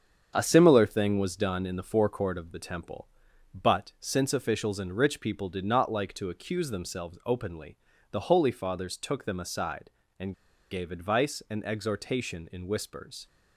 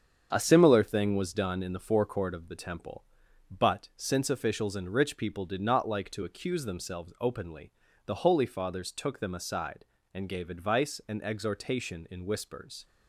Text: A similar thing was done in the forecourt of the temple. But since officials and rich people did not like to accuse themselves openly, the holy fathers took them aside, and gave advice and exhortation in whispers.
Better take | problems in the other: second | starts louder than the rest; strong; until 1.3 s; 7.5 dB; strong in the second // pauses between "and" and "gave"; at 10.3 s; 0.37 s long

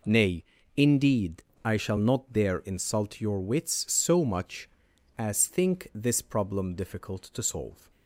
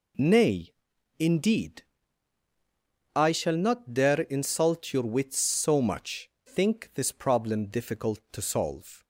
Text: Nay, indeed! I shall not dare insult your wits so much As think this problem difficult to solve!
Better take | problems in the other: first | skips "As"; at 6.3 s

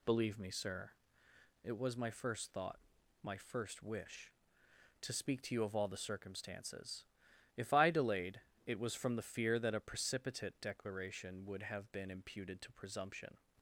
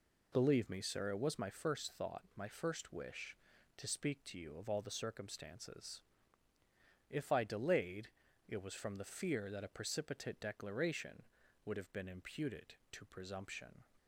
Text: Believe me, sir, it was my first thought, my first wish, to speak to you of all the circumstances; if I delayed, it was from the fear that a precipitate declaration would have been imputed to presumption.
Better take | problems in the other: neither | none

